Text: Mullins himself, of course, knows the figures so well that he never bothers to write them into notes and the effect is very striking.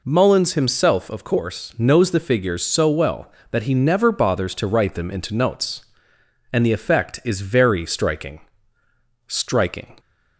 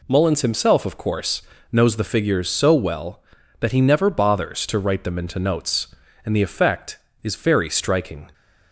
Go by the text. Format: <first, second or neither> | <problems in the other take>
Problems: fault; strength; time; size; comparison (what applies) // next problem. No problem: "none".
second | says "striking" twice; at 9.2 s